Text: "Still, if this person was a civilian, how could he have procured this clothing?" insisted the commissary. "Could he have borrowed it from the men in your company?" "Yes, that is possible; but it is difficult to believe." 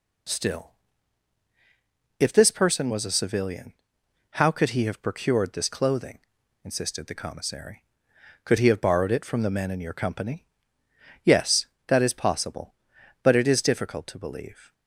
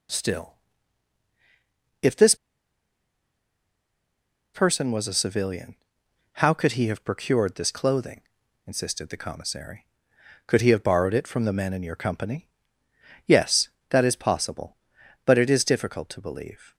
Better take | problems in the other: first | pauses between "this" and "person"; strong; at 2.3 s; 2.1 s long

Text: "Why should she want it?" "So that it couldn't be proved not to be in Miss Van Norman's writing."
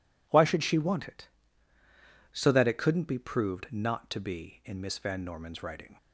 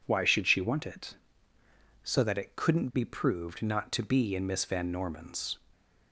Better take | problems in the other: first | stops before "writing"; at 5.7 s

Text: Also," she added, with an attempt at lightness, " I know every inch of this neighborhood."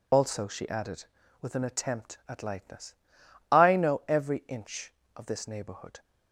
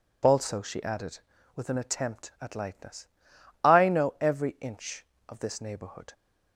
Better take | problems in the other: second | loses the start of "Also"; at 0.1 s; 35 ms

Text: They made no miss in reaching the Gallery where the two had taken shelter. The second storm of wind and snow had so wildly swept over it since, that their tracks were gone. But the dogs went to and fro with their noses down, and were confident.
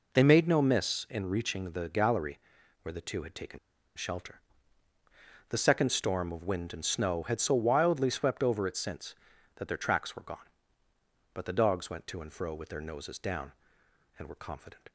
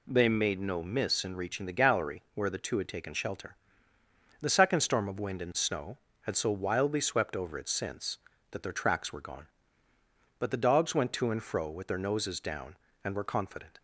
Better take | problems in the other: second | pauses between "Gallery" and "where"; at 2.3 s; 0.44 s long // pauses between "taken" and "shelter"; at 3.5 s; 0.38 s long

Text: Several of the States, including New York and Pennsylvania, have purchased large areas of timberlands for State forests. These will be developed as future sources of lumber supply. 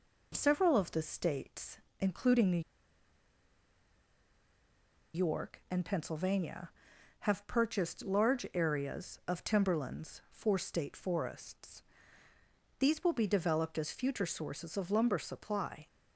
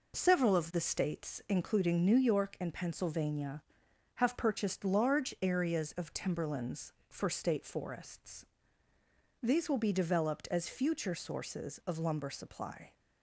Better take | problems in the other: second | pauses between "New" and "York"; strong; at 2.6 s; 2.5 s long

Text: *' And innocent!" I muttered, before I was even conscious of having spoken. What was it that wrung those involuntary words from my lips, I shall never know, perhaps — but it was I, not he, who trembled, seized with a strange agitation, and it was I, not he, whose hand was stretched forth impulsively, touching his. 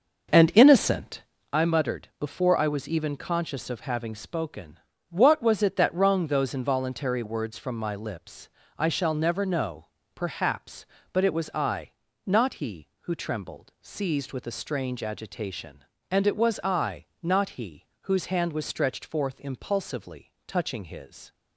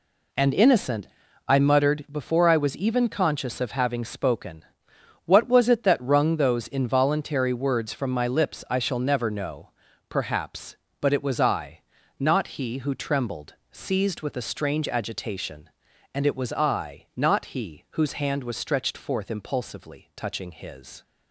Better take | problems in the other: second | starts louder than the rest; noticeable; until 1.4 s; 6 dB

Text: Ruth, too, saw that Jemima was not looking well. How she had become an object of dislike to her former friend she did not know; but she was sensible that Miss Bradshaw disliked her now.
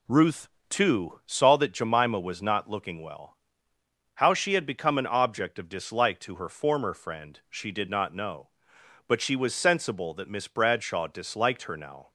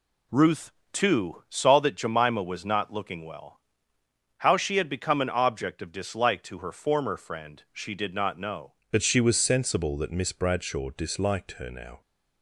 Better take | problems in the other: first | changes voice at "but"; from 8.9 s on; 3.1 s long

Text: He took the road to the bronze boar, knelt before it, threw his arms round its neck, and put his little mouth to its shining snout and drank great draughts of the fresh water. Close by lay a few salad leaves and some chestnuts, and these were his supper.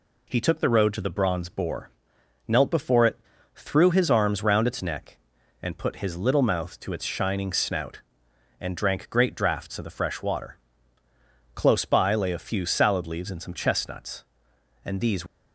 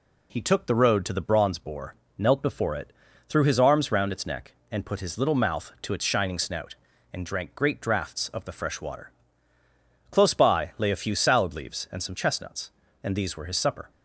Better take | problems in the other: second | stops before "were his supper"; at 15.2 s

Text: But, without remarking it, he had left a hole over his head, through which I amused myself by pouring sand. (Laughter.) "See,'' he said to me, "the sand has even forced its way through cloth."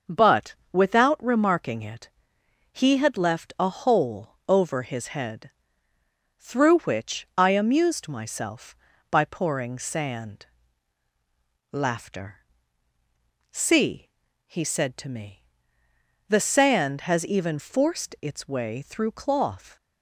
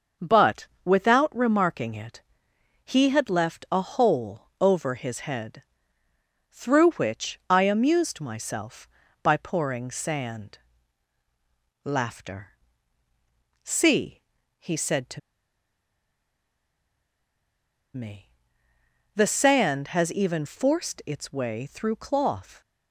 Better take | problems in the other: first | starts louder than the rest; until 1.3 s; 6 dB; also in the first // pauses between "to" and "me"; strong; at 15.1 s; 2.7 s long

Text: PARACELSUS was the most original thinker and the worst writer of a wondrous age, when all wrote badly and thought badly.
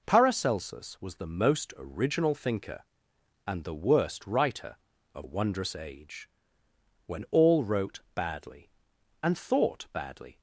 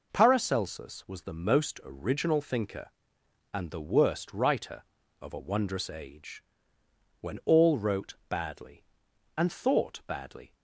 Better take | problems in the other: second | skips "a"; at 5.2 s

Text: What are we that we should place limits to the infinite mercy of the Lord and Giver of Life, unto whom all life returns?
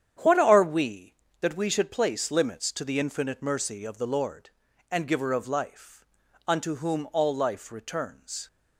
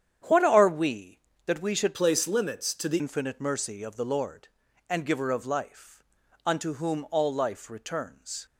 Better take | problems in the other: first | starts louder than the rest; strong; until 1.5 s; 9 dB; strong in the first // changes voice from "place" to "the"; from 1.9 to 2.9 s; 1.0 s long

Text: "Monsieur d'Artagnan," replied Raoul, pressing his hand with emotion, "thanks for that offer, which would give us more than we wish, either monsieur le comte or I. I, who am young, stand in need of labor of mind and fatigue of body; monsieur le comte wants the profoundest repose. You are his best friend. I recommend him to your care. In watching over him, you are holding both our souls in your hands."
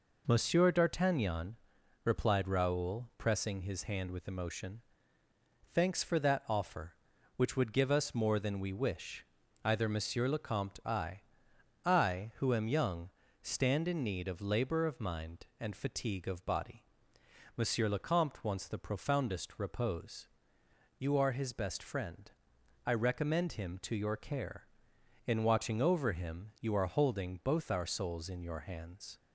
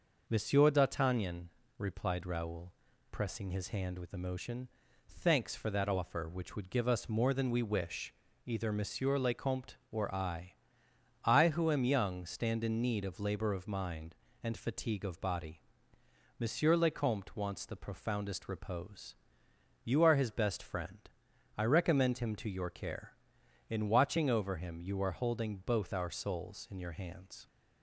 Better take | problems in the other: second | skips "or"; at 10.8 s

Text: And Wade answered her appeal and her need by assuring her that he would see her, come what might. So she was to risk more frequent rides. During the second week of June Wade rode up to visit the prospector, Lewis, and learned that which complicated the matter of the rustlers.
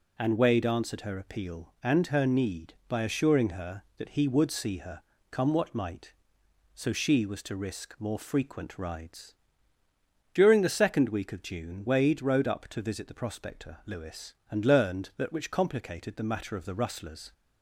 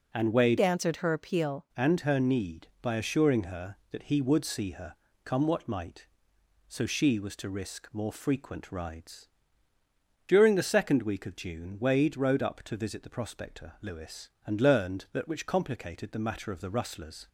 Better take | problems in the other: first | changes voice from "answered" to "appeal"; from 0.5 to 1.6 s; 1.1 s long

